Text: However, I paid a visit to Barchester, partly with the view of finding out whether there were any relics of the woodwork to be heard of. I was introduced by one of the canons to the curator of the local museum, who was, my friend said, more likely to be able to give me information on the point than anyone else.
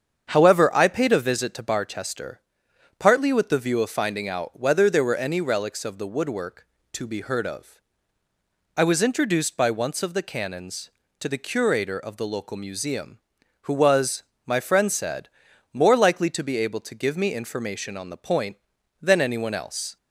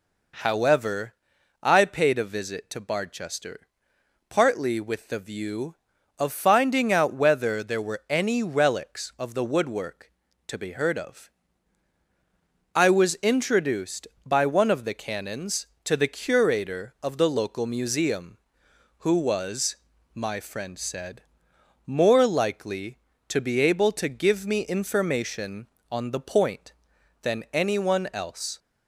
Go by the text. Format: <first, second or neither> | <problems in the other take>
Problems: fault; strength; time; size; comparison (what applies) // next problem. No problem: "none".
second | starts louder than the rest; strong; until 1.3 s; 7.5 dB // says "once" for "one"; at 9.7 s